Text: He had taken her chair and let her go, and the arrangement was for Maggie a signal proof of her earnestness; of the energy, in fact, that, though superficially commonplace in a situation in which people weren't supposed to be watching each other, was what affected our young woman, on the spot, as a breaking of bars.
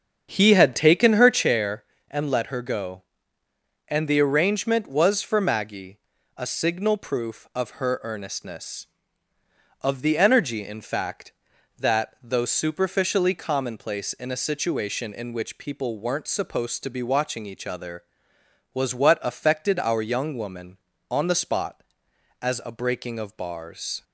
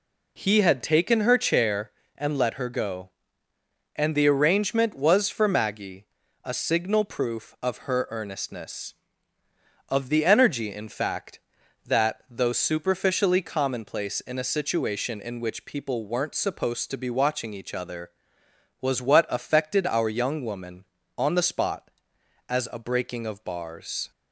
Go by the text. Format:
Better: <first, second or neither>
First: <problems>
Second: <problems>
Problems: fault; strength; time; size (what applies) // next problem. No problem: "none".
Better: second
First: starts louder than the rest; strong; until 1.5 s; 8 dB // pauses between "Maggie" and "a"; at 5.9 s; 0.40 s long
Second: pauses between "Maggie" and "a"; at 6.0 s; 0.40 s long